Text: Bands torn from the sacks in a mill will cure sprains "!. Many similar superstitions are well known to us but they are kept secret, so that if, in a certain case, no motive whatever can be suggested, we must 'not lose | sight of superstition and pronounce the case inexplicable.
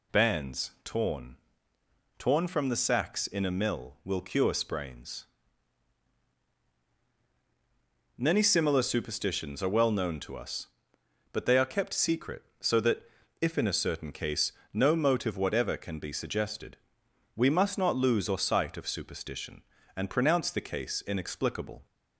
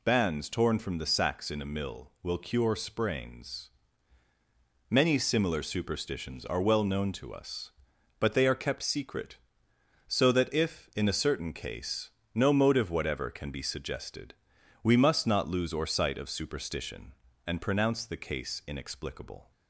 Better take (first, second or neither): second